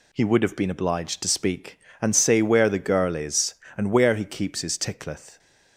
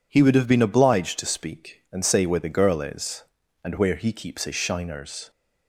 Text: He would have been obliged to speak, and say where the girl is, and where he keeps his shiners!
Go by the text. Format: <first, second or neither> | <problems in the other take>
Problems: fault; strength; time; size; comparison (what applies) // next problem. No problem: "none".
second | says "tickleth" for "shiners"; at 4.7 s